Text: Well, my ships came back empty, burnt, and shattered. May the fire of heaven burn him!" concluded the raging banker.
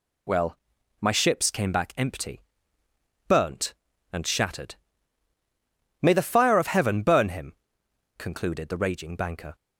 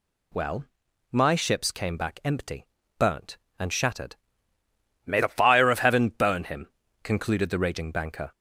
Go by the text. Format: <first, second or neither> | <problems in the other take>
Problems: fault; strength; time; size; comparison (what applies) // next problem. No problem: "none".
neither | none